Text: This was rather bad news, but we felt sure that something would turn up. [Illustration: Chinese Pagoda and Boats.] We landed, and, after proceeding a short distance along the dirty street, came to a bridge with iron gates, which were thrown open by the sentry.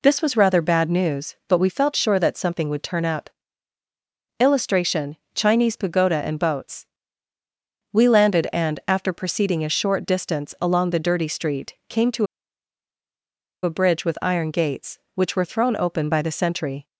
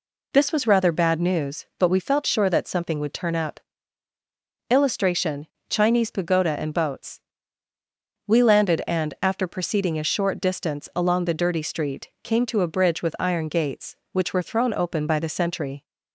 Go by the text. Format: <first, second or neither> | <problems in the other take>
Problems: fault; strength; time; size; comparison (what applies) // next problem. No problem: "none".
second | pauses between "to" and "a"; strong; at 12.2 s; 1.3 s long